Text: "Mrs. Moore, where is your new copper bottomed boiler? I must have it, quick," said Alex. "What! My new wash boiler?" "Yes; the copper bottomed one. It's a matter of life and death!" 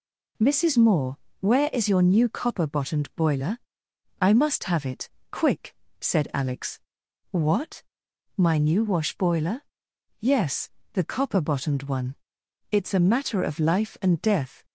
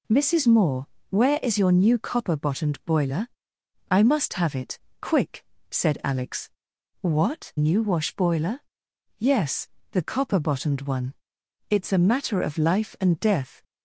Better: first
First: none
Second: skips "My"; at 7.5 s

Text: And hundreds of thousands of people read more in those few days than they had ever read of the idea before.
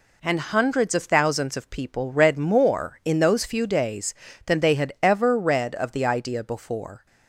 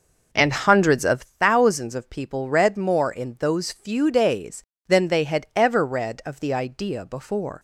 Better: first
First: none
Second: starts louder than the rest; noticeable; until 1.2 s; 5 dB

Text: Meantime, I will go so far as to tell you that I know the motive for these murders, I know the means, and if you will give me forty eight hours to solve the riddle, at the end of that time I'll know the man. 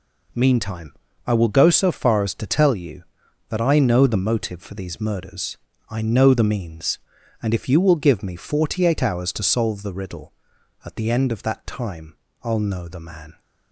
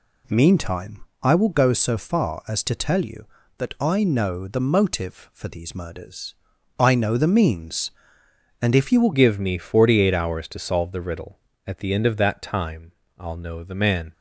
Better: first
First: pauses between "time" and "I'll"; slight; at 12.1 s; 0.28 s long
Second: changes voice at "give"; from 9.1 s on; 5.0 s long // pauses between "time" and "I'll"; slight; at 12.9 s; 0.26 s long

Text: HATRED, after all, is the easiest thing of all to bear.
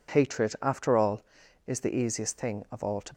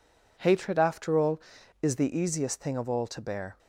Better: second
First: stops before "bear"; at 3.1 s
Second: none

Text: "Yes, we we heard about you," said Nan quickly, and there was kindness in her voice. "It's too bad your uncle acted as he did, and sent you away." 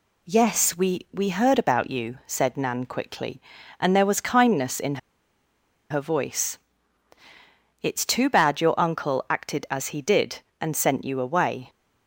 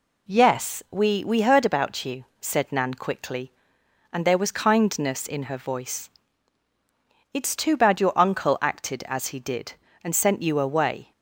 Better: second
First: pauses between "in" and "her"; noticeable; at 4.9 s; 0.93 s long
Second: none

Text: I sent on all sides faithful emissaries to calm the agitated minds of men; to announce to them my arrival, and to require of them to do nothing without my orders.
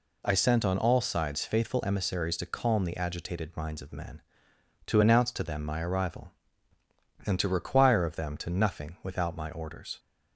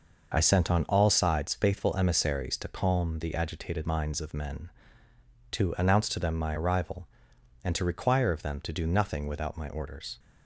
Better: second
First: skips "do"; at 8.4 s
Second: none

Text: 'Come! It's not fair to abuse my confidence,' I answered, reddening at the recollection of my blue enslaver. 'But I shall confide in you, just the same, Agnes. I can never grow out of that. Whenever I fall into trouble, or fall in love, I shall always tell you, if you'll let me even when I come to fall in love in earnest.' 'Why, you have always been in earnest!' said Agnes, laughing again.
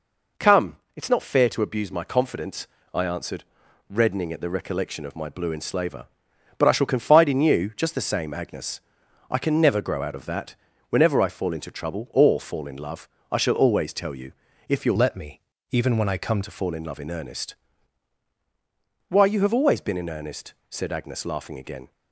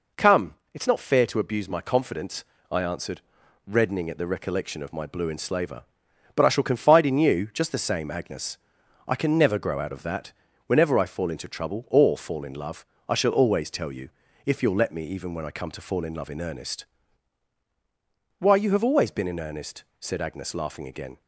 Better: second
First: changes voice from "let" to "come"; from 14.9 to 16.4 s; 1.5 s long // pauses between "me" and "even"; slight; at 15.4 s; 0.30 s long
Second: none

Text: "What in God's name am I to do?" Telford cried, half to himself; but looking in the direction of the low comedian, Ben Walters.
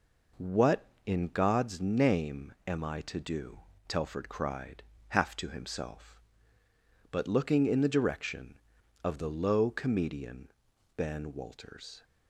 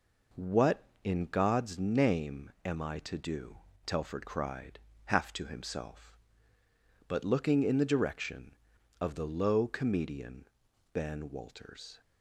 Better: neither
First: none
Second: none

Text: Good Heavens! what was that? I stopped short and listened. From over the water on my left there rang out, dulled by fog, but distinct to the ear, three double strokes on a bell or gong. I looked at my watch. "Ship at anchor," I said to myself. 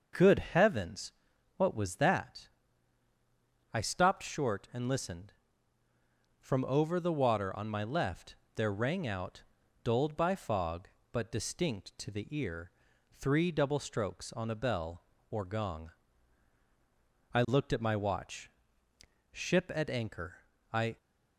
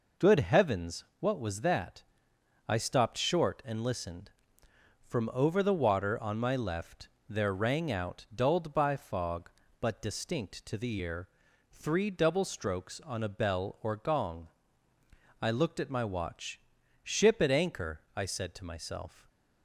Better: second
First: starts louder than the rest; noticeable; until 1.6 s; 6 dB // pauses between "left" and "there"; slight; at 8.3 s; 0.18 s long // stops before "said to myself"; at 20.9 s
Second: pauses between "left" and "there"; slight; at 7.0 s; 0.18 s long

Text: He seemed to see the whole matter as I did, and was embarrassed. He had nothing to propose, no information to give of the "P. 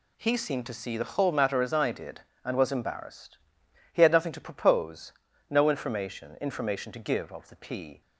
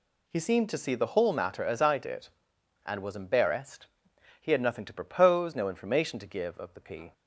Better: second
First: says "information" twice; at 6.4 s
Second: none

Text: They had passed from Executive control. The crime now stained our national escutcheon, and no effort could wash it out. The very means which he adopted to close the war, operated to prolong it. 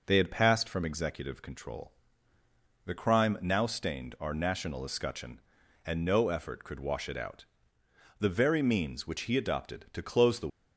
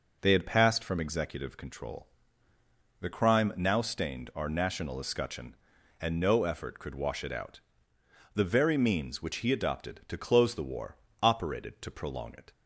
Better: second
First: stops before "war operated to prolong it"; at 10.4 s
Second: none

